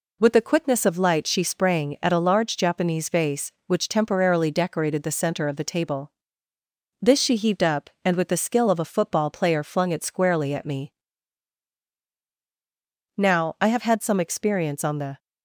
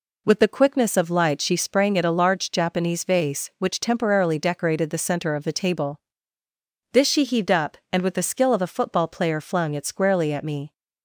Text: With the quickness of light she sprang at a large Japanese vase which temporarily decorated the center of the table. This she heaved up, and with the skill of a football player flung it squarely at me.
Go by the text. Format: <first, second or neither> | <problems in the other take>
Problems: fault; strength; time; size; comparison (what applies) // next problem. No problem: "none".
second | goes on to say "Now I have had some experience on the"; strong; from 13.1 s on; 2.0 s long